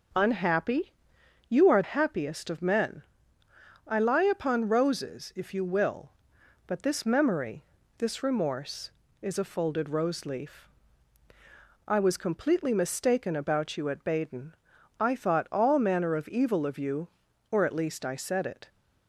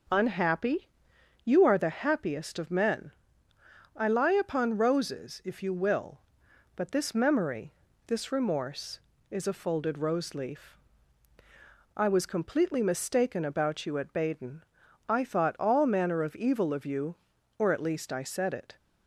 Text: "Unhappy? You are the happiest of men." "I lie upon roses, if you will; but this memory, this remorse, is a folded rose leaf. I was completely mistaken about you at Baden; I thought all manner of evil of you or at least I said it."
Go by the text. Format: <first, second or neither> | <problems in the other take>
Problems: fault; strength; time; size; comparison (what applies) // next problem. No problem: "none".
second | skips "the"; at 1.8 s